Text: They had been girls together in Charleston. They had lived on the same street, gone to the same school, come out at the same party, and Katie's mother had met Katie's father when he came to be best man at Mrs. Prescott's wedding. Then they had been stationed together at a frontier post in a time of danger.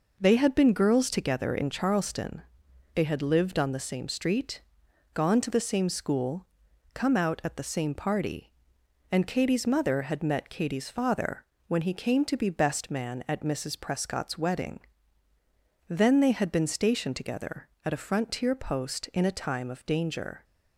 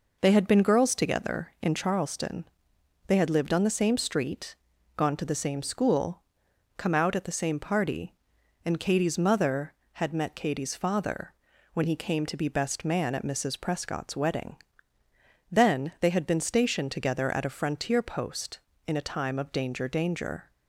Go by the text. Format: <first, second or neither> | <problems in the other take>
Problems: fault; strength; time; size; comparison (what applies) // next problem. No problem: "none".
first | pauses between "father" and "when"; at 11.3 s; 0.40 s long; slight in the first // says "danger" twice; at 19.8 s